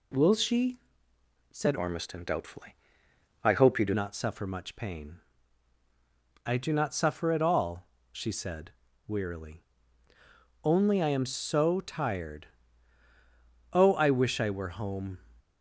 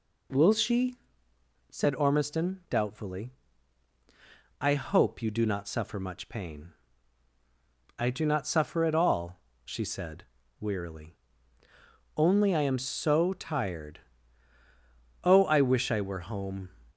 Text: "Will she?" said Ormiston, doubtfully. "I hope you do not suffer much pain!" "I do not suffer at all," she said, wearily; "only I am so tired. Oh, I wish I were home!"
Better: second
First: changes voice from "Ormiston" to "do"; from 1.7 to 3.9 s; 2.2 s long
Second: none

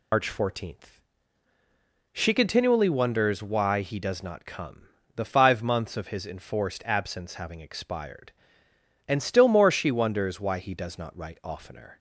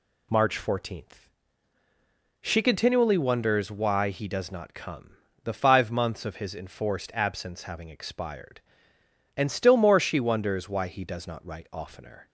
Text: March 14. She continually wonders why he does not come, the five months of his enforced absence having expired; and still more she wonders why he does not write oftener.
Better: second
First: loses the start of "March"; at 0.1 s; 100 ms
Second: none

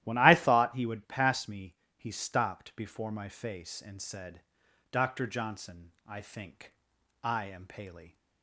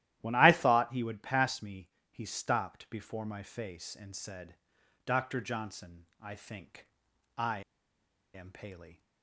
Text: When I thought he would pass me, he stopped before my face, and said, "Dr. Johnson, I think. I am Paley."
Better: first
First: starts louder than the rest; strong; until 1.0 s; 13.5 dB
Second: starts louder than the rest; strong; until 1.2 s; 13.5 dB // pauses between "I" and "am"; noticeable; at 7.6 s; 0.73 s long

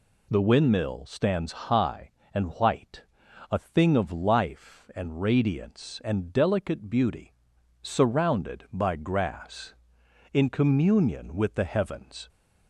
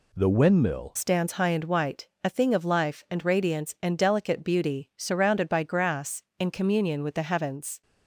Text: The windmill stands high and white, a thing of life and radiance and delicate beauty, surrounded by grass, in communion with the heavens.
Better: first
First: none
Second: changes voice at "stands"; from 0.9 s on; 6.9 s long

